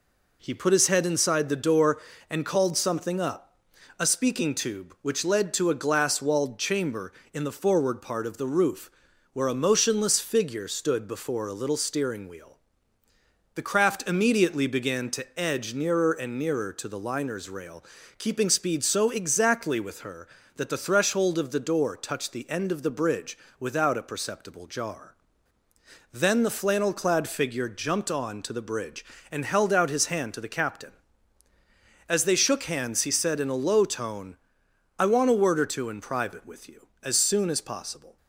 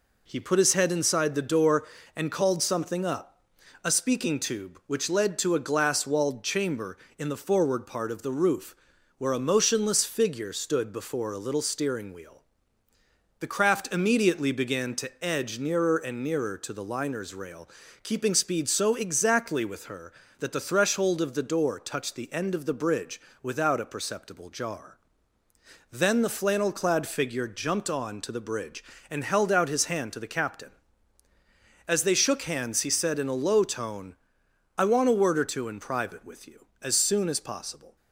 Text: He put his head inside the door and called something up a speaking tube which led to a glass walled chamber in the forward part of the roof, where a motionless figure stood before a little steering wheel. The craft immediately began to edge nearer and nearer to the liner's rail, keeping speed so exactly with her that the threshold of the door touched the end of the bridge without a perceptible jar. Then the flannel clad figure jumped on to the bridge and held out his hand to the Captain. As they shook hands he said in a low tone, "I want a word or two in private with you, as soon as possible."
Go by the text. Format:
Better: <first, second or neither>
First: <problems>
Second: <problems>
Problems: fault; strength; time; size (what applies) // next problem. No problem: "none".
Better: neither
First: pauses between "up" and "a"; at 3.5 s; 0.40 s long // pauses between "bridge" and "without"; slight; at 23.3 s; 0.22 s long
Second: pauses between "up" and "a"; at 3.4 s; 0.40 s long // pauses between "bridge" and "without"; slight; at 23.1 s; 0.22 s long